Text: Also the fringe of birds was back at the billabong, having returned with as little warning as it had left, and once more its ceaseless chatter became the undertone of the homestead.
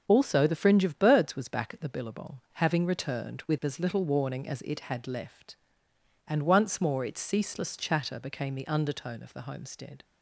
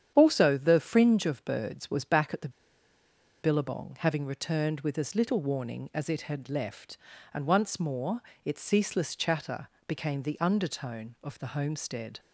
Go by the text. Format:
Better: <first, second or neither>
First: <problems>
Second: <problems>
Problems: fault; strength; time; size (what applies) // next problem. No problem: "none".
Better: first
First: starts louder than the rest; until 1.0 s; 6.5 dB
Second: starts louder than the rest; strong; until 1.1 s; 9 dB // pauses between "the" and "billabong"; noticeable; at 2.4 s; 0.93 s long // pauses between "more" and "its"; slight; at 8.2 s; 0.22 s long // pauses between "chatter" and "became"; slight; at 9.6 s; 0.20 s long